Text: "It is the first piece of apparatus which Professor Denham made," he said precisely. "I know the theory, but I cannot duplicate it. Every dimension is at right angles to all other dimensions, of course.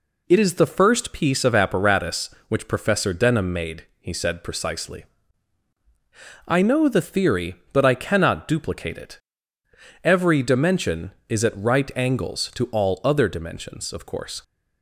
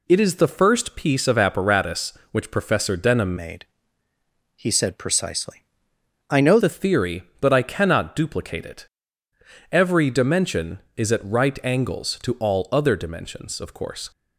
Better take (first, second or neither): first